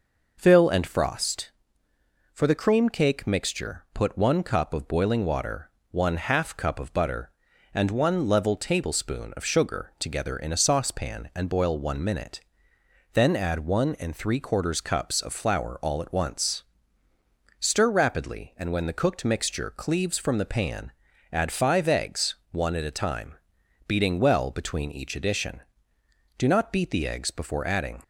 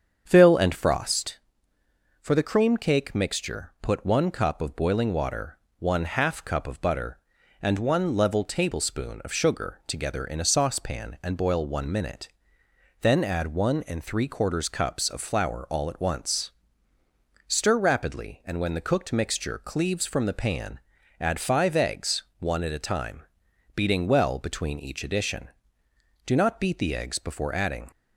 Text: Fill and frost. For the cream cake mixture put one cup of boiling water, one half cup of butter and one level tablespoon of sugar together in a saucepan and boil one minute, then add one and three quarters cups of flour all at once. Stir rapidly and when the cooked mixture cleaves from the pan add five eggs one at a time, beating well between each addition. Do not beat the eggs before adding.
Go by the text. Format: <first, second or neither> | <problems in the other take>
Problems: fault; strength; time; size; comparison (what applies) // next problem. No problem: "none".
first | starts louder than the rest; strong; until 1.4 s; 7.5 dB // pauses between "pan" and "add"; at 20.8 s; 0.40 s long; also in the first // pauses between "eggs" and "one"; slight; at 22.2 s; 0.16 s long; slight in the first